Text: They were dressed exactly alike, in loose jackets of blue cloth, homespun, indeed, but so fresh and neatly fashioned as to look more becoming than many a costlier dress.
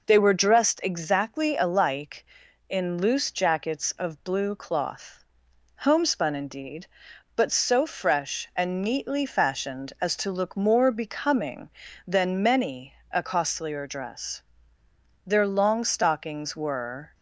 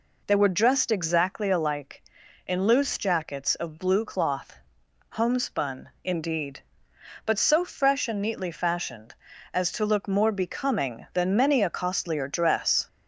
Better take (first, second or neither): second